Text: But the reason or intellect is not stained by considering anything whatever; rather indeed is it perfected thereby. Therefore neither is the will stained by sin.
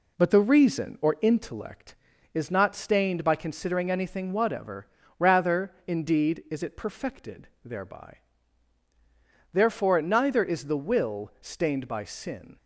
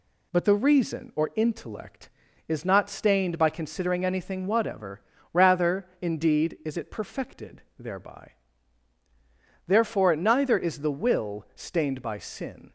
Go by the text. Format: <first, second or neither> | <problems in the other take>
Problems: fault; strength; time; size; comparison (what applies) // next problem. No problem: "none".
second | starts louder than the rest; slight; until 1.6 s; 3 dB // pauses between "perfected" and "thereby"; slight; at 7.4 s; 0.18 s long; slight in the second